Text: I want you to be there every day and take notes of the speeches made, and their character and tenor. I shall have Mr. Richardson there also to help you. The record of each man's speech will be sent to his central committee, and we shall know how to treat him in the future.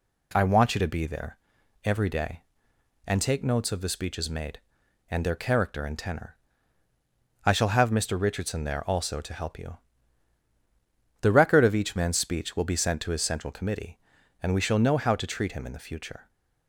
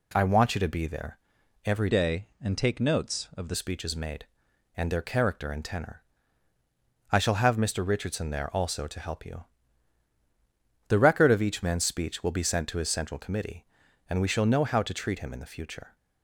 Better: first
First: pauses between "there" and "every"; noticeable; at 1.3 s; 0.46 s long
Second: pauses between "there" and "every"; noticeable; at 1.1 s; 0.46 s long // changes voice from "day" to "the"; from 1.8 to 3.5 s; 1.7 s long

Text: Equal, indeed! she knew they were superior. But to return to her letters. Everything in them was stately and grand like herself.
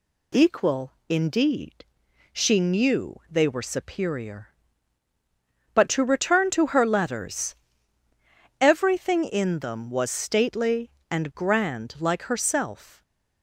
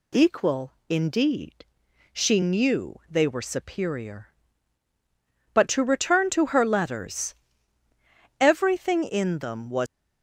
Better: first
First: none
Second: stops before "stately and grand like herself"; at 9.8 s

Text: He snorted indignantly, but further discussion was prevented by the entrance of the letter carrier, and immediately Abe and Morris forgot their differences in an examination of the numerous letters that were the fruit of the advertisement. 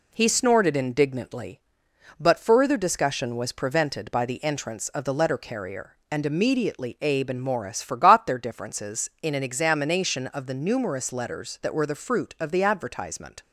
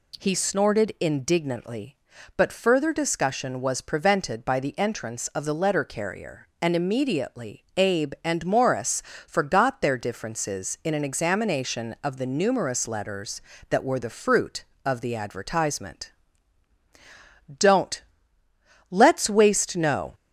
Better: first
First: none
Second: pauses between "Morris" and "forgot"; slight; at 9.0 s; 0.24 s long // goes on to say "Don't let's waste no"; strong; from 17.5 s on; 2.5 s long

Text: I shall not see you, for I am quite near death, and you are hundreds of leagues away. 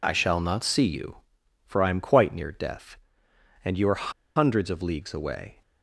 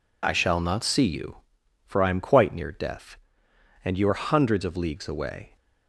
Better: second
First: pauses between "are" and "hundreds"; slight; at 4.1 s; 0.24 s long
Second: none

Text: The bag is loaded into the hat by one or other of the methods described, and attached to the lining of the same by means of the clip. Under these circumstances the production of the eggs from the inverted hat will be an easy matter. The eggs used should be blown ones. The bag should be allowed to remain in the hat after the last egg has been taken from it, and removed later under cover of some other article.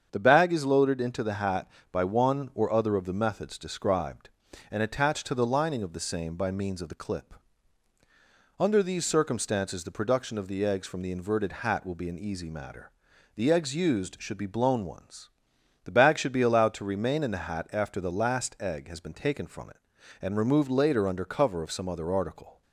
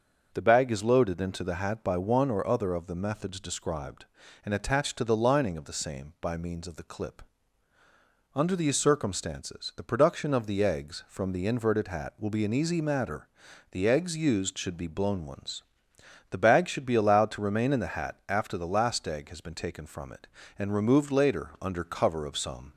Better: first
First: starts louder than the rest; strong; until 1.1 s; 7.5 dB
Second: starts louder than the rest; until 1.3 s; 6 dB // stops before "other article"; at 22.7 s

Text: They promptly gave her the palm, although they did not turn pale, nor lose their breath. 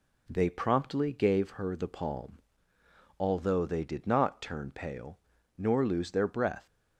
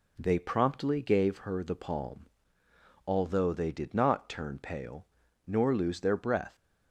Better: neither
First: none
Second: none

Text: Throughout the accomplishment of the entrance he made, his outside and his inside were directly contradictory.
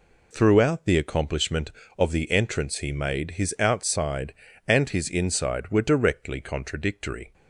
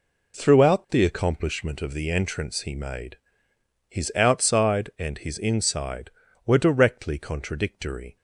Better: neither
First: none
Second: none

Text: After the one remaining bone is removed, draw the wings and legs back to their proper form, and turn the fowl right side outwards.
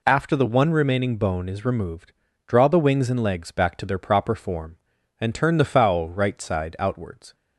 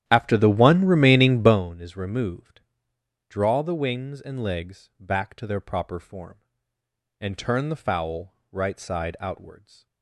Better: first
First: none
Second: starts louder than the rest; strong; until 1.6 s; 11 dB // pauses between "fowl" and "right"; slight; at 8.3 s; 0.20 s long

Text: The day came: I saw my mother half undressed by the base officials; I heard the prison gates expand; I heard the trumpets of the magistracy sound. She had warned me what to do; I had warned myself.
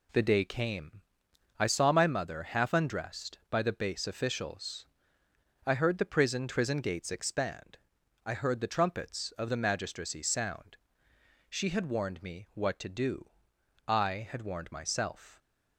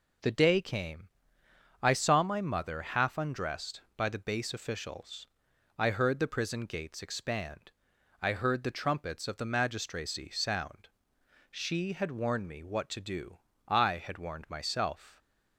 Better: second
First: says "prison" twice; at 6.4 s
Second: none

